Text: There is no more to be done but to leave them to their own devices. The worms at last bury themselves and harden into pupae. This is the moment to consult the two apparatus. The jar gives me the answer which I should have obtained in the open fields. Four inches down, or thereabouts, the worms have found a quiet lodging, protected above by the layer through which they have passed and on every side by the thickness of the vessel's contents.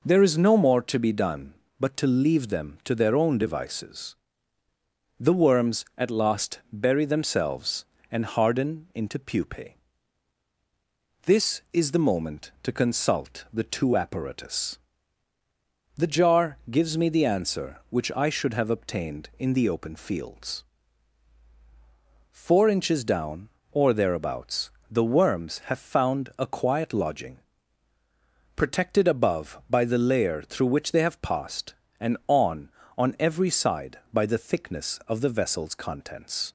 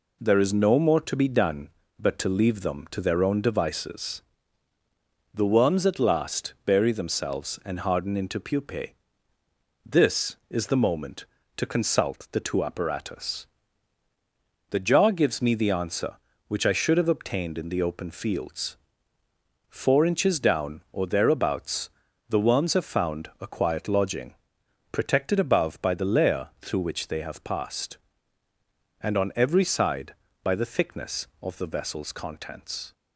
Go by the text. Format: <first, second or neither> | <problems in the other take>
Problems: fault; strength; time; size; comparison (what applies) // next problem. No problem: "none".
second | says "on" twice; at 32.9 s